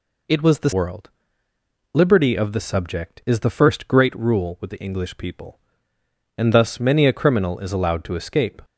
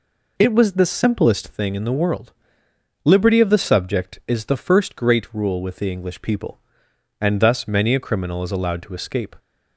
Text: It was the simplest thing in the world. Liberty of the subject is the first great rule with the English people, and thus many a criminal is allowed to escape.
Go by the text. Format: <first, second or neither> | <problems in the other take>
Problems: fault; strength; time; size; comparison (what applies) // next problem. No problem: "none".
second | skips "simplest thing in the"; at 0.7 s